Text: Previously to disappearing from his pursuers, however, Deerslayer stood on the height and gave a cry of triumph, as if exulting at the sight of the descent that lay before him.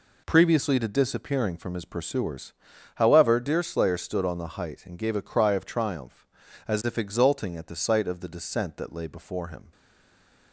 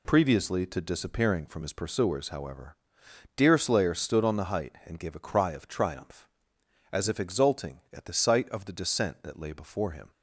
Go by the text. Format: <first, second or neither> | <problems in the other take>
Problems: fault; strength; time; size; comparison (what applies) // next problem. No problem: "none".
second | stays silent after the last word; slight; from 9.7 s on; 0.8 s long